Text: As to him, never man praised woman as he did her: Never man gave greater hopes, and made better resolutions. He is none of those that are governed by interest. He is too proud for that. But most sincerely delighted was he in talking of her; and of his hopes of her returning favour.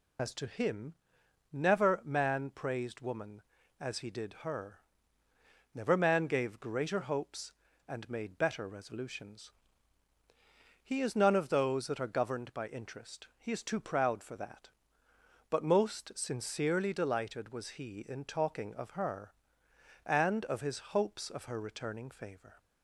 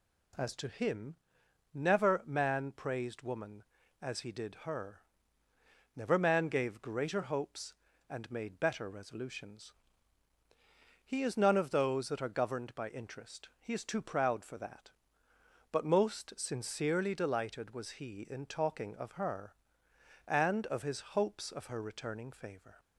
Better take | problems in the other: second | loses the start of "As"; at 0.1 s; 80 ms

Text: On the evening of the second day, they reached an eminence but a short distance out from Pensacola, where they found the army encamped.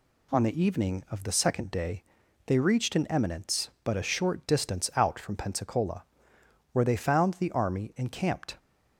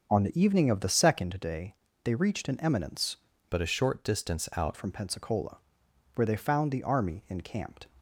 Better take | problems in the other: first | starts louder than the rest; until 1.1 s; 6.5 dB // changes voice from "but" to "out"; from 3.5 to 4.7 s; 1.2 s long

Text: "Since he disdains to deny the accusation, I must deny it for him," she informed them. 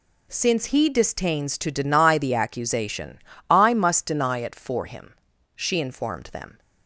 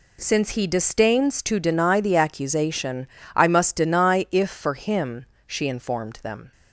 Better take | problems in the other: first | says "if" for "it"; at 4.3 s

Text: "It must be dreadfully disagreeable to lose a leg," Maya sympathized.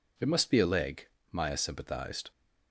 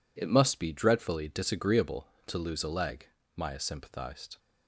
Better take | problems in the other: second | skips "dreadfully disagreeable to lose"; at 0.5 s

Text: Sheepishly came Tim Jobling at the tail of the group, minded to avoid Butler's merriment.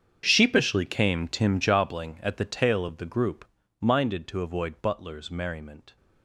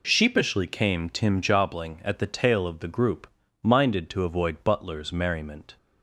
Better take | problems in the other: second | gets quieter; strong; throughout; 18 dB

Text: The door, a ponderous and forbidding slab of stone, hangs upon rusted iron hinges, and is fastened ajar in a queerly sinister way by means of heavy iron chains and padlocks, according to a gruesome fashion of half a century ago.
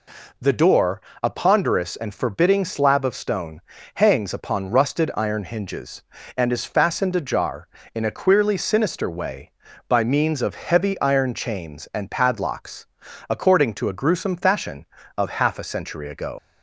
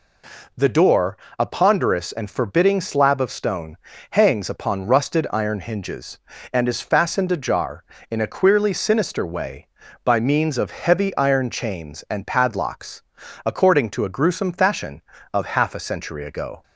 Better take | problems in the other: second | leaves "ago" unfinished; at 16.3 s; 80 ms

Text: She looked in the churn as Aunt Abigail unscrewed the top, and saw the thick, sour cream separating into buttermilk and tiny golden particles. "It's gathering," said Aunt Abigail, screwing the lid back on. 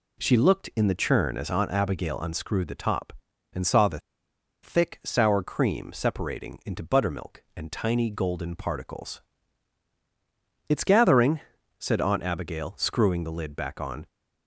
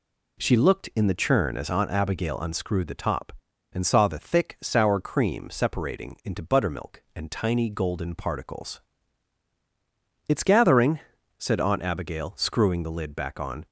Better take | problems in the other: second | pauses between "the" and "thick"; noticeable; at 4.0 s; 0.62 s long

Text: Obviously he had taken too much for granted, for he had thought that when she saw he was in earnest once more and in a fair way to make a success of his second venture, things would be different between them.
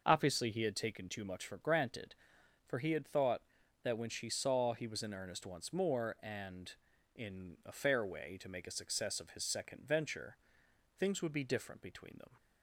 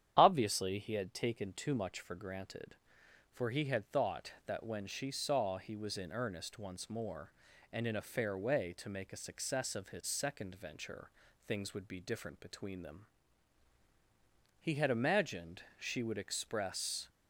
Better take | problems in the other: first | starts louder than the rest; strong; until 1.1 s; 9.5 dB // goes on to say "He had imagined she would express"; strong; from 14.6 s on; 2.4 s long

